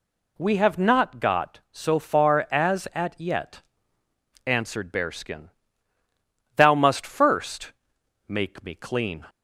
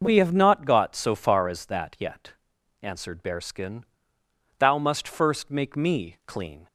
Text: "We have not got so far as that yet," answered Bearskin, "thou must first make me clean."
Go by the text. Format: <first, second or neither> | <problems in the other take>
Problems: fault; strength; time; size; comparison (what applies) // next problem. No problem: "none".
second | says "at" for "that"; at 2.9 s // pauses between "first" and "make"; noticeable; at 7.7 s; 0.56 s long